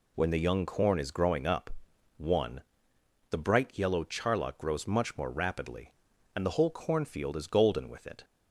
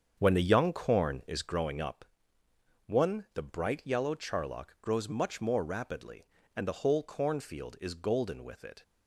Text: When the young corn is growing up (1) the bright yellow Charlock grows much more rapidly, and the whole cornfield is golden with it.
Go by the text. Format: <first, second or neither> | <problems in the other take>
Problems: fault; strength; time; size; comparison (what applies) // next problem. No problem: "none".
first | starts louder than the rest; strong; until 1.7 s; 7.5 dB